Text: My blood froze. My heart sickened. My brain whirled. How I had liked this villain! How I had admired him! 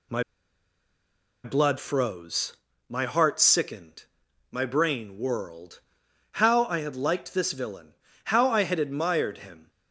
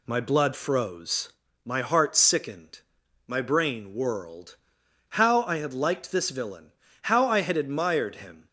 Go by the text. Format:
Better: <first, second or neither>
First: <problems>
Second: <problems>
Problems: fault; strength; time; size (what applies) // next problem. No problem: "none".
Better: second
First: pauses between "My" and "blood"; at 0.2 s; 1.2 s long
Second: none